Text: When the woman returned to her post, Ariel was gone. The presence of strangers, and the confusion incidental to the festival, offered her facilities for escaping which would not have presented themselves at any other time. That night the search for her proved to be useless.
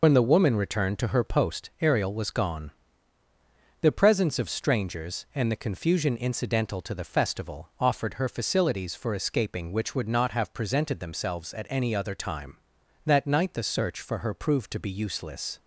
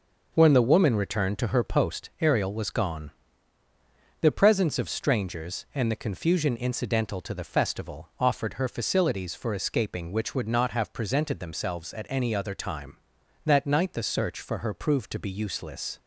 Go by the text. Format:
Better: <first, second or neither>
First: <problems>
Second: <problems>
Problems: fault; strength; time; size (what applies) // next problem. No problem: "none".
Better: second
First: loses the start of "When"; at 0.0 s; 80 ms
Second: none